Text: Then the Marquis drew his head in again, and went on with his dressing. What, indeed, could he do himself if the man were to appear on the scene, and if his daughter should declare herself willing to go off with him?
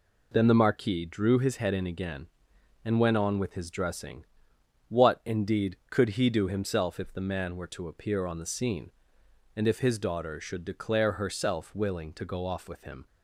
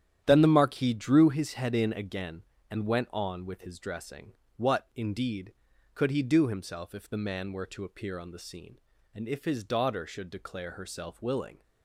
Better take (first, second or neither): first